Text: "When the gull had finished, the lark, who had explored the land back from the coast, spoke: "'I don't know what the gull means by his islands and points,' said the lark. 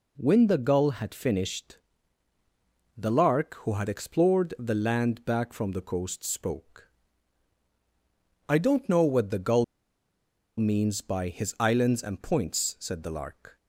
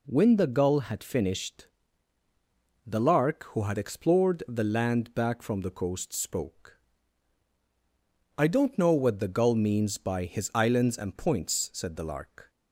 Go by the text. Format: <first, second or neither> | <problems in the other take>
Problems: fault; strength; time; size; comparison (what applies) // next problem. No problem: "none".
second | pauses between "gull" and "means"; noticeable; at 9.6 s; 0.94 s long